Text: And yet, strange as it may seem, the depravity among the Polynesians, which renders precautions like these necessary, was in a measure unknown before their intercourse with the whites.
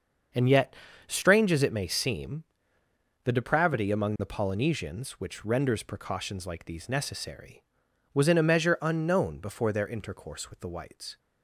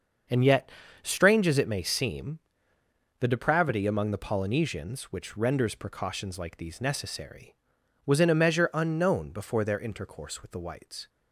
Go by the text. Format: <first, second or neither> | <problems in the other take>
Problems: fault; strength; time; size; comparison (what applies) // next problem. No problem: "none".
neither | starts louder than the rest; the same in both